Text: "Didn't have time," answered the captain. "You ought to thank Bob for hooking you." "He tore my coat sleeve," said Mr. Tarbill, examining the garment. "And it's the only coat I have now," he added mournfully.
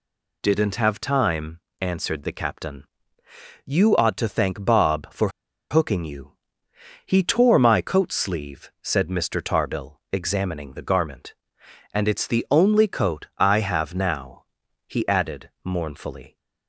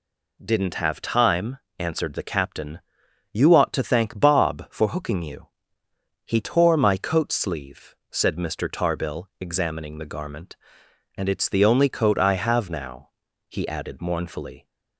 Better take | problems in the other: second | pauses between "for" and "hooking"; at 5.2 s; 0.41 s long

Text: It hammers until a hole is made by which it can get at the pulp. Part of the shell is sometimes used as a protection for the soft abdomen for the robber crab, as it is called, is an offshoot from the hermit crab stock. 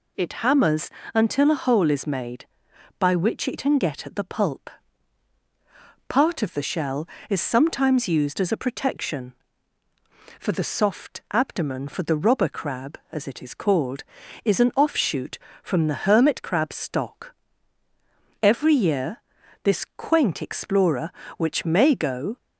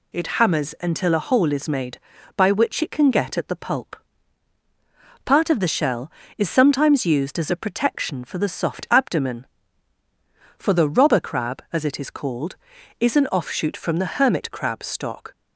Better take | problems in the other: second | pauses between "hammers" and "until"; slight; at 0.8 s; 0.24 s long // goes on to say "Every year this quaint explorer which may go"; strong; from 18.4 s on; 3.9 s long

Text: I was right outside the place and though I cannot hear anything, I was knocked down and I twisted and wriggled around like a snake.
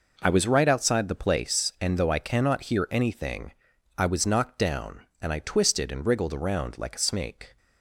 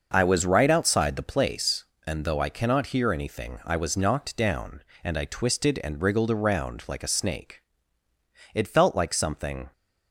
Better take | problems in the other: first | starts louder than the rest; noticeable; until 1.1 s; 6 dB // goes on to say "It felt like something"; noticeable; from 8.5 s on; 1.2 s long

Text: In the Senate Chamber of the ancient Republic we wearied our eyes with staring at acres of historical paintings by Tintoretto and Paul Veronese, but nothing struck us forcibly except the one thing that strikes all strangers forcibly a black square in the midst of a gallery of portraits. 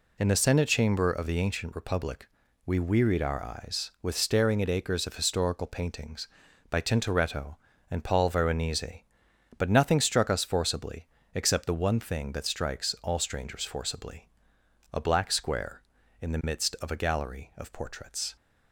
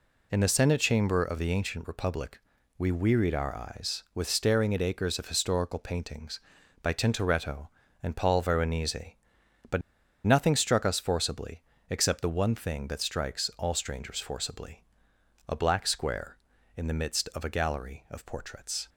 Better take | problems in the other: first | pauses between "Republic" and "we"; at 2.3 s; 0.40 s long; also in the first // pauses between "but" and "nothing"; at 9.8 s; 0.45 s long // pauses between "forcibly" and "except"; slight; at 11.6 s; 0.26 s long; slight in the first // pauses between "forcibly" and "a"; noticeable; at 14.8 s; 0.66 s long; noticeable in the first

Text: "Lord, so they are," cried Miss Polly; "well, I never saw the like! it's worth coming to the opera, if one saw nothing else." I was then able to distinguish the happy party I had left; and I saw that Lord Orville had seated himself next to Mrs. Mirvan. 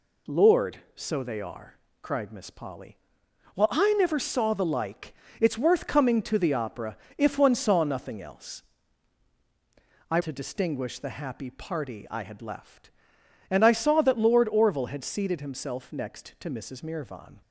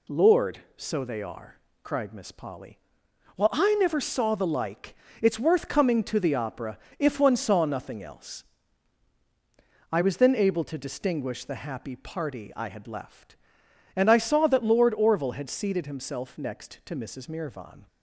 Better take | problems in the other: second | skips "was then able"; at 10.1 s

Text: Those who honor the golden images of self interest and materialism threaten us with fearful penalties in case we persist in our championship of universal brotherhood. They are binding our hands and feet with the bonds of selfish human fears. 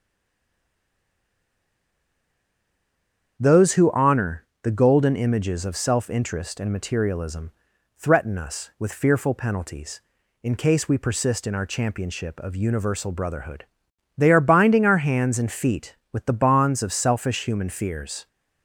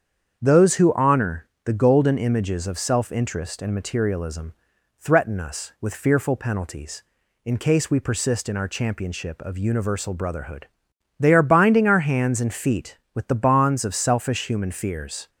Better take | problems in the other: second | stays silent before the first word; strong; until 3.3 s; 3.3 s long // starts louder than the rest; strong; until 4.4 s; 8 dB; strong in the second // pauses between "honor" and "the"; slight; at 4.4 s; 0.16 s long; slight in the second // pauses between "materialism" and "threaten"; noticeable; at 7.5 s; 0.46 s long; noticeable in the second

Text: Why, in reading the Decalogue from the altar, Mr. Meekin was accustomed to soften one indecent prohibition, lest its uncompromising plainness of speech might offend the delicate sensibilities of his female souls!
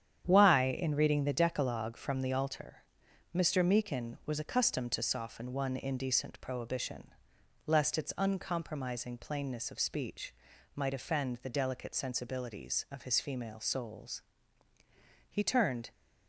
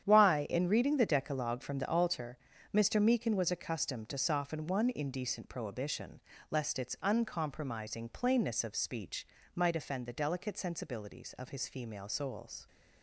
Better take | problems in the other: second | starts louder than the rest; strong; until 1.2 s; 9 dB; strong in the second // pauses between "speech" and "might"; at 10.3 s; 0.40 s long; slight in the second // goes on to say "He turned"; noticeable; from 15.2 s on; 0.62 s long

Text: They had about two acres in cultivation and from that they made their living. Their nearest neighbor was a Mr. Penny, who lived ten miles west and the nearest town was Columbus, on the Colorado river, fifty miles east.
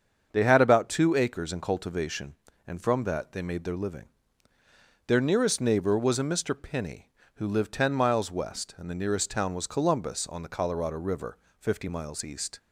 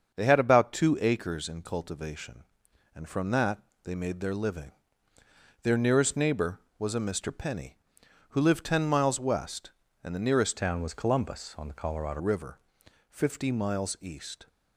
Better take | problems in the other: first | starts louder than the rest; until 1.1 s; 7 dB; strong in the first // pauses between "that" and "they"; slight; at 3.5 s; 0.26 s long // changes voice from "town" to "Colorado"; from 10.5 to 12.2 s; 1.7 s long

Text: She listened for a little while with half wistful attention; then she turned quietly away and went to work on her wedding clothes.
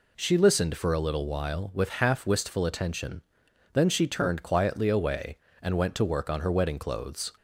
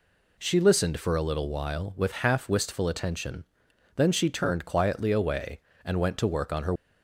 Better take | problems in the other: first | stops before "wedding clothes"; at 6.7 s

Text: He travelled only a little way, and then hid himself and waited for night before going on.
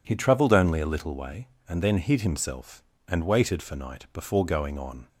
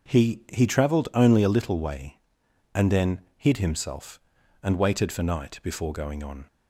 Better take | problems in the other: first | says "He" twice; at 0.4 s // pauses between "then" and "hid"; slight; at 3.2 s; 0.16 s long

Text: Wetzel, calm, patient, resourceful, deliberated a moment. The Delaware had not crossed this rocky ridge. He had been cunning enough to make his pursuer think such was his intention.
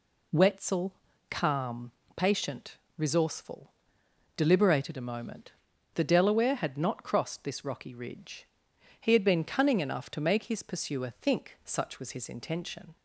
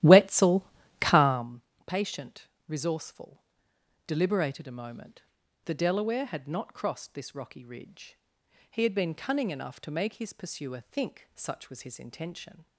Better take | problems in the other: first | starts louder than the rest; strong; until 1.5 s; 14 dB

